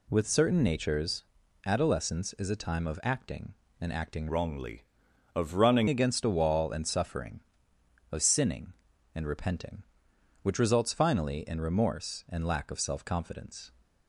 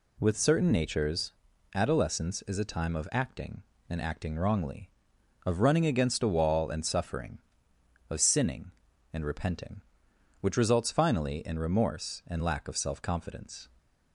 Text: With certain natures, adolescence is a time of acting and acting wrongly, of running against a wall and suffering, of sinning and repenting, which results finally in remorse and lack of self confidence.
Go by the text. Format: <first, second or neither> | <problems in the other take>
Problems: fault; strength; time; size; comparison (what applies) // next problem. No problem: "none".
second | changes voice from "wrongly" to "running"; from 4.2 to 5.8 s; 1.6 s long